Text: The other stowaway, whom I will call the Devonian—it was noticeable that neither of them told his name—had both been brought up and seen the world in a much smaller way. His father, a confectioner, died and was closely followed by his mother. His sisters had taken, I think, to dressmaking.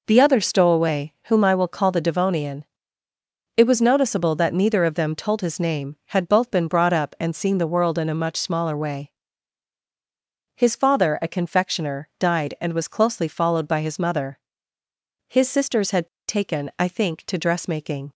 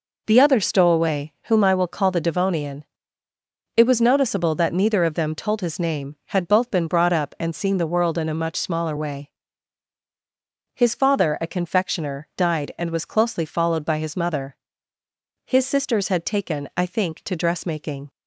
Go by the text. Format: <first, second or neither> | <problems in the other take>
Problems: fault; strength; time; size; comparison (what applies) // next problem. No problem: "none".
second | pauses between "had" and "taken"; slight; at 16.0 s; 0.19 s long